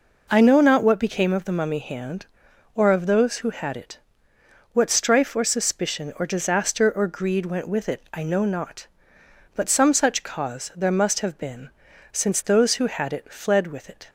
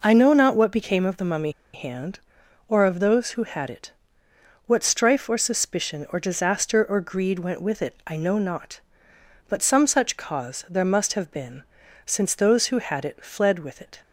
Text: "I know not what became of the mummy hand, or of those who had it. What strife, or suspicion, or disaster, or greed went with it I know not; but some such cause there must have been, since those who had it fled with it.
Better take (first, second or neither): first